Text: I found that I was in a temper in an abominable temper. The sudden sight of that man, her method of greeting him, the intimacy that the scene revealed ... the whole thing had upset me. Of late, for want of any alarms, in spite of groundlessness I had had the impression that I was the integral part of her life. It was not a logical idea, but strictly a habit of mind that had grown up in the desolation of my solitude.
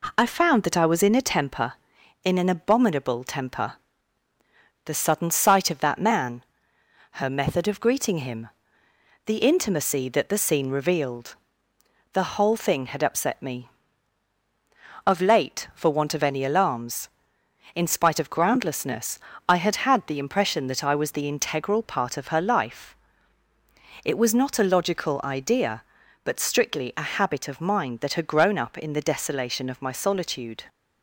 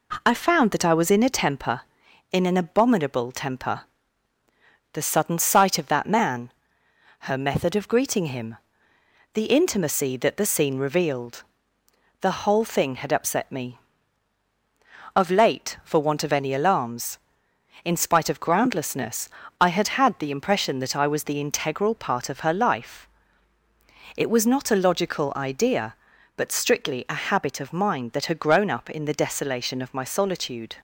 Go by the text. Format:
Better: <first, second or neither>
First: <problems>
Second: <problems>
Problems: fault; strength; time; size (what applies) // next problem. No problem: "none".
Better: neither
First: pauses between "groundlessness" and "I"; slight; at 19.1 s; 0.28 s long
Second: pauses between "groundlessness" and "I"; slight; at 19.2 s; 0.30 s long